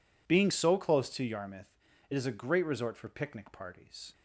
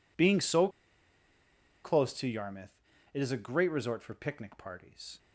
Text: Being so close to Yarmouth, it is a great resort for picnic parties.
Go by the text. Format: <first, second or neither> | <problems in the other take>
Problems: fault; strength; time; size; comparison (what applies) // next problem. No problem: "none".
first | pauses between "so" and "close"; at 0.6 s; 1.1 s long